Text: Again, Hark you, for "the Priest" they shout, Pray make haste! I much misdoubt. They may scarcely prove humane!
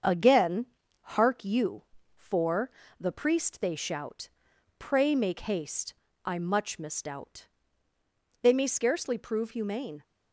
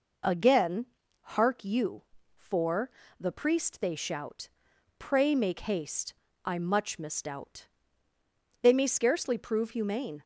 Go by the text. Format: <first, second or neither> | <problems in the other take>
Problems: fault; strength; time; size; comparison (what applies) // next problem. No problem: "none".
second | gets quieter; slight; throughout; 3.5 dB // pauses between "for" and "the"; slight; at 2.6 s; 0.32 s long; slight in the second